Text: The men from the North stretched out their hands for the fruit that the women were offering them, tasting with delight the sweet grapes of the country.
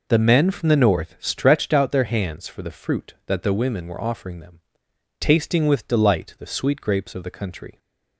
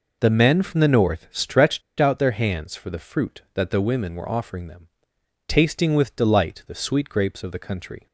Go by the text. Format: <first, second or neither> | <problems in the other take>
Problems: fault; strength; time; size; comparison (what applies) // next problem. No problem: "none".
first | pauses between "stretched" and "out"; slight; at 1.8 s; 0.16 s long